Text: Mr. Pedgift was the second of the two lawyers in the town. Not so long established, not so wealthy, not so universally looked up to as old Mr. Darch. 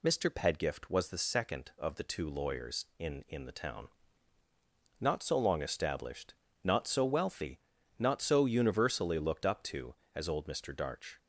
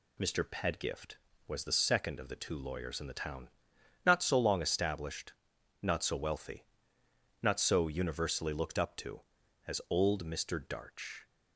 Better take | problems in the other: second | says "in" twice; at 3.2 s

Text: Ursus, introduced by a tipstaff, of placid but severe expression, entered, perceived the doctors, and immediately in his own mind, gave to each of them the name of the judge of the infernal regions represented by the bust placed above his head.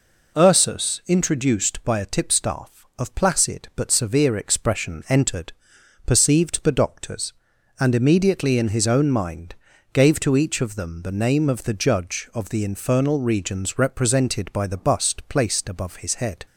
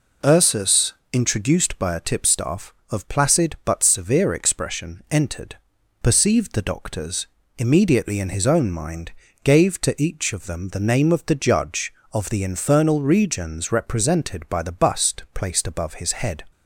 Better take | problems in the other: first | skips "and"; at 7.4 s

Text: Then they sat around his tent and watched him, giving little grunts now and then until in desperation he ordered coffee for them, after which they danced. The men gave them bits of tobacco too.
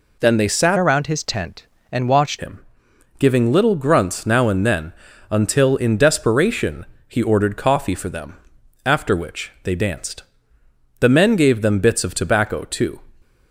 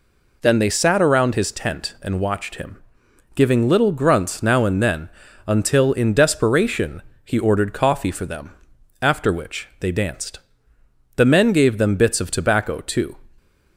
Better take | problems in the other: second | changes voice from "around" to "watched"; from 0.7 to 2.3 s; 1.6 s long // pauses between "then" and "until"; at 4.9 s; 0.38 s long; also in the second // pauses between "desperation" and "he"; slight; at 6.8 s; 0.22 s long; slight in the second

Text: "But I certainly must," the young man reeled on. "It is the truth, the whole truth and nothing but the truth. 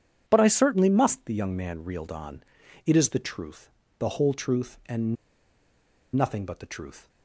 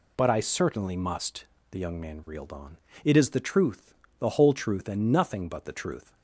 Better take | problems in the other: second | pauses between "and" and "nothing"; at 5.1 s; 1.0 s long

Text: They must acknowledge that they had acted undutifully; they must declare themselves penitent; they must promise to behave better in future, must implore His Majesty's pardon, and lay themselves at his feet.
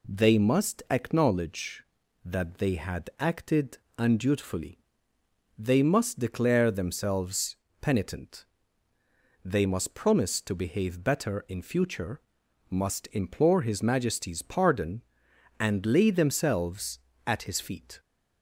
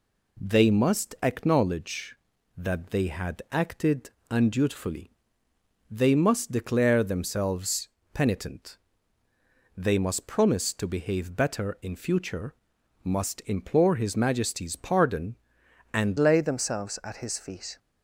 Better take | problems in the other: first | pauses between "acted" and "undutifully"; slight; at 4.0 s; 0.20 s long; slight in the first // pauses between "themselves" and "penitent"; slight; at 7.8 s; 0.26 s long; slight in the first // changes voice at "lay"; from 16.1 s on; 1.6 s long

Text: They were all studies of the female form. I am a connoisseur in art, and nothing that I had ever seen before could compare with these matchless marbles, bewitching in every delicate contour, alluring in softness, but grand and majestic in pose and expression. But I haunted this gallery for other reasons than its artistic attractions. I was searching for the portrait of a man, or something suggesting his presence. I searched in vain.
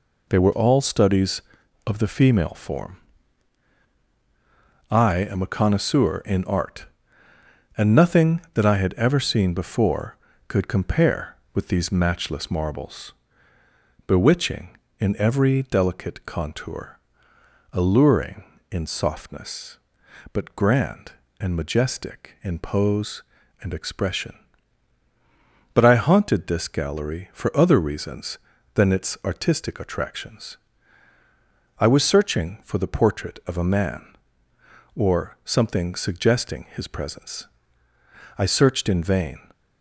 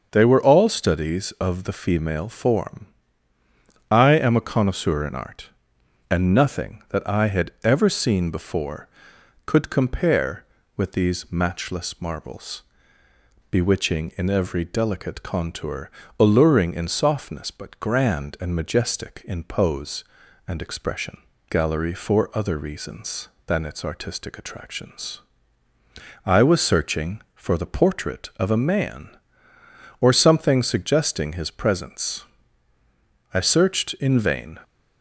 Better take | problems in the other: first | starts louder than the rest; until 1.1 s; 6.5 dB // skips "But I haunted this"; at 21.3 s

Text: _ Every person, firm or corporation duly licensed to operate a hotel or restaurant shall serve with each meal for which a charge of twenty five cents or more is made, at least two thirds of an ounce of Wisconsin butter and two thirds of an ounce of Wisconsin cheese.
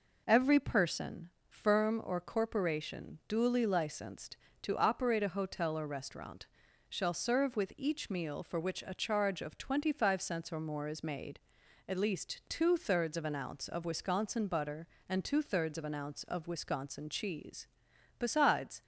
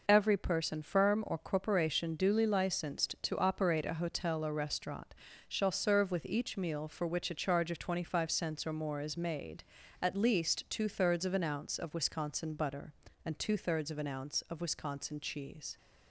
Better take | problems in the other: second | pauses between "restaurant" and "shall"; at 6.4 s; 0.42 s long; slight in the second // goes on to say "Besides"; noticeable; from 18.1 s on; 0.64 s long

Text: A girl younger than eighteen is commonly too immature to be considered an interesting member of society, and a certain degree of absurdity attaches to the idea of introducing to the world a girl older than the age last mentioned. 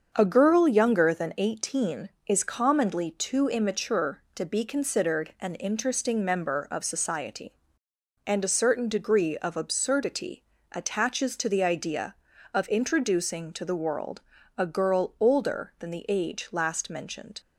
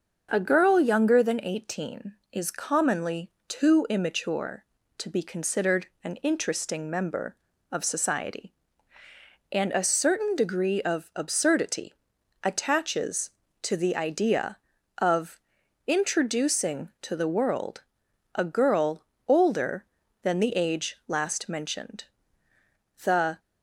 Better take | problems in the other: first | starts louder than the rest; until 1.3 s; 6.5 dB; also in the first // pauses between "commonly" and "too"; slight; at 3.3 s; 0.16 s long // pauses between "considered" and "an"; slight; at 5.8 s; 0.16 s long // pauses between "absurdity" and "attaches"; noticeable; at 11.9 s; 0.50 s long; slight in the first // pauses between "of" and "introducing"; noticeable; at 15.3 s; 0.48 s long // pauses between "world" and "a"; noticeable; at 17.8 s; 0.54 s long; also in the first // pauses between "girl" and "older"; slight; at 19.0 s; 0.26 s long // goes on to say "The"; slight; from 23.0 s on; 0.36 s long

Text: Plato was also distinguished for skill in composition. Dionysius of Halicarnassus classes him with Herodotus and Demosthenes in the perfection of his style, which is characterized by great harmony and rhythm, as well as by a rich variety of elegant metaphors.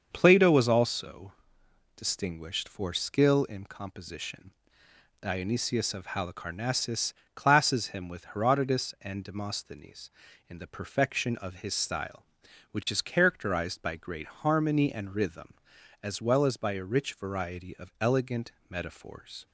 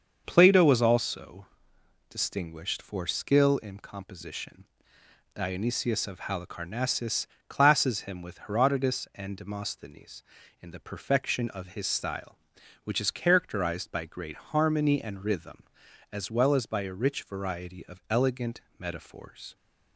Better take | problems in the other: neither | starts louder than the rest; the same in both // pauses between "also" and "distinguished"; noticeable; the same in both // pauses between "Halicarnassus" and "classes"; slight; the same in both // pauses between "elegant" and "metaphors"; slight; the same in both

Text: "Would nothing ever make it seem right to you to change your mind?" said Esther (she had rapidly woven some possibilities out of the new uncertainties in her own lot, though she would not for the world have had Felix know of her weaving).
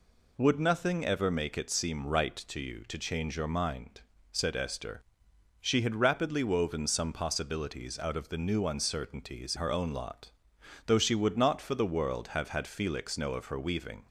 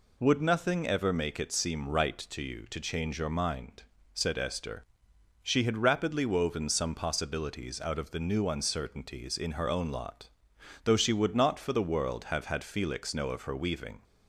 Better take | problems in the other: second | skips "in"; at 9.5 s

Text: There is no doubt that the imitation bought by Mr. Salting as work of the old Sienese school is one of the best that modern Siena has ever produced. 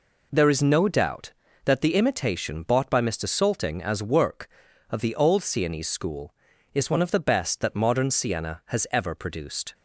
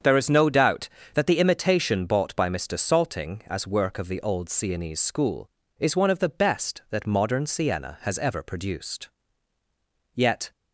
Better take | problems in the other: first | starts louder than the rest; strong; until 1.2 s; 7.5 dB // goes on to say "Yet"; slight; from 10.1 s on; 0.36 s long

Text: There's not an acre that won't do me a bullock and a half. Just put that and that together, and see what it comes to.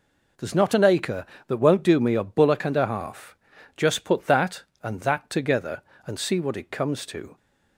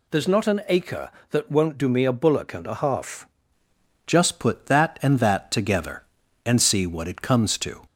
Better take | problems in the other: first | changes voice at "Just"; from 4.0 s on; 3.8 s long

